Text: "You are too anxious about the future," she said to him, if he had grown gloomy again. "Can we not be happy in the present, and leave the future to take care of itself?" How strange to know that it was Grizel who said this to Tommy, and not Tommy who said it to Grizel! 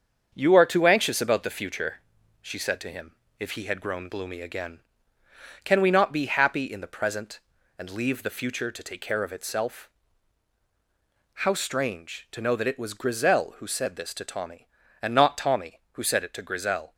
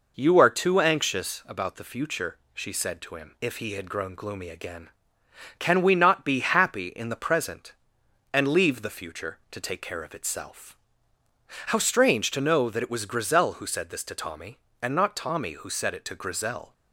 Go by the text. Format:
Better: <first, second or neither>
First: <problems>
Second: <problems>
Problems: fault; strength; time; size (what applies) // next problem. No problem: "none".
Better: second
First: gets quieter; noticeable; throughout; 5.5 dB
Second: none